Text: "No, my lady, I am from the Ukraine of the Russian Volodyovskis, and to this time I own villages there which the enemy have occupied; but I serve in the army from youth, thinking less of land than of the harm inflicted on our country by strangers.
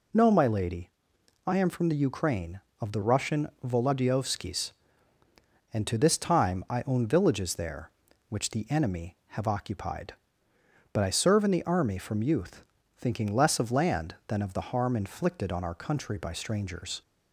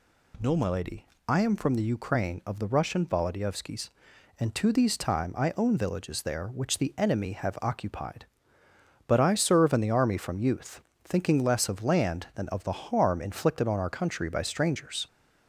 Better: first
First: none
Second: says "these" for "this"; at 4.7 s

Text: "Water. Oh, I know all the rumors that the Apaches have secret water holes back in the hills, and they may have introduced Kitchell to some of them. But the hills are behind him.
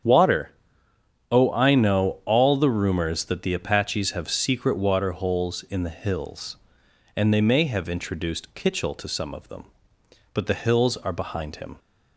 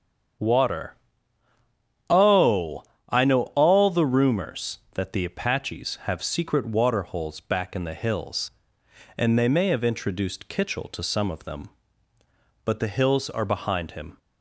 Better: second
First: starts louder than the rest; strong; until 1.8 s; 8.5 dB // skips "back"; at 5.6 s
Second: starts louder than the rest; strong; until 2.5 s; 8 dB

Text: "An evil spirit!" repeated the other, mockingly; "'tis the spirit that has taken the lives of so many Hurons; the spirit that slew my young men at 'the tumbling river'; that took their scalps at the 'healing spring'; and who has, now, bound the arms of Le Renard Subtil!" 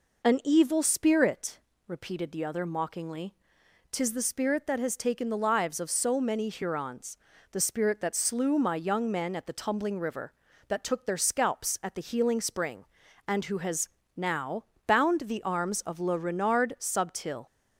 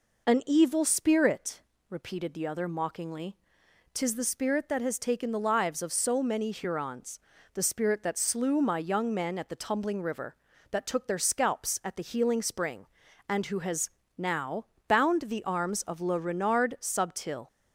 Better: neither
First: none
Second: none

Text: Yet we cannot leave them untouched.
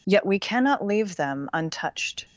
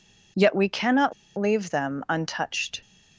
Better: first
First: none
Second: pauses between "cannot" and "leave"; slight; at 1.1 s; 0.25 s long

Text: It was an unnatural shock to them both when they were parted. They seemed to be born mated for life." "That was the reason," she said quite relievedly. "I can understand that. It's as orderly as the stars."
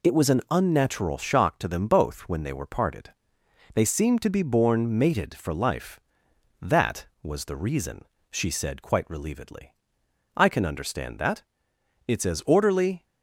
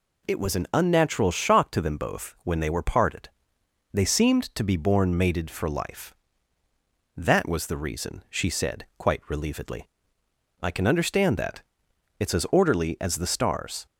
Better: second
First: stops before "as the stars"; at 13.0 s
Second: none

